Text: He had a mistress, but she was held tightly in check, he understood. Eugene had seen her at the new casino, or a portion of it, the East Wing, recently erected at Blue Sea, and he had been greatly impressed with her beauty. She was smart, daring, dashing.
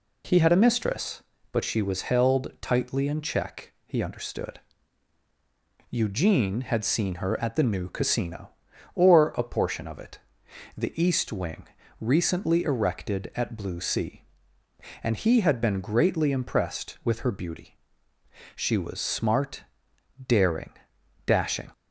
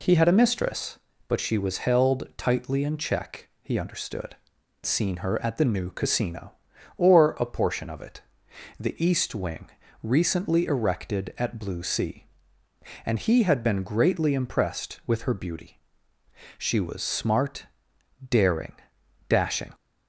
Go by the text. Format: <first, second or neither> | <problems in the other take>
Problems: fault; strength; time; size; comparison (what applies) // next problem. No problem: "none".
first | skips "Eugene had"; at 4.5 s